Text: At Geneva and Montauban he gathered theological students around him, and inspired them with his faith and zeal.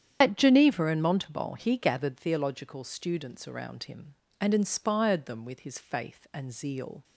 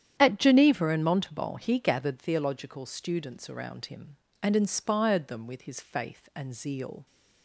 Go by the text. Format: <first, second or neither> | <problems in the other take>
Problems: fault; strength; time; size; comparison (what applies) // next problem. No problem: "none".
second | loses the start of "At"; at 0.2 s; 30 ms // starts louder than the rest; strong; until 1.2 s; 9 dB; strong in the second